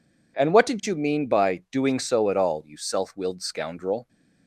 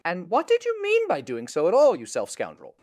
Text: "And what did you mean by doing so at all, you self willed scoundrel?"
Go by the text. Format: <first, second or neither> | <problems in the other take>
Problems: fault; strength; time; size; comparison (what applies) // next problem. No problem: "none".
first | skips "willed"; at 2.2 s